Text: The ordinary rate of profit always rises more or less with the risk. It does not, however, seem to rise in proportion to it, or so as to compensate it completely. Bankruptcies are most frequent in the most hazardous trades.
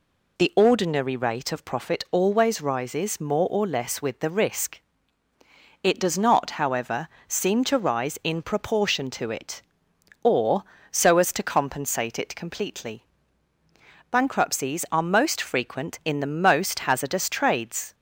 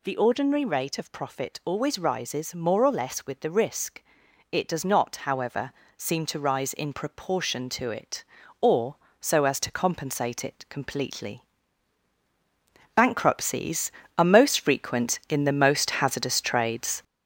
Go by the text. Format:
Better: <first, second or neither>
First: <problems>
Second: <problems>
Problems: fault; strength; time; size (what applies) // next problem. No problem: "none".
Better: first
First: none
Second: gets louder; noticeable; throughout; 6 dB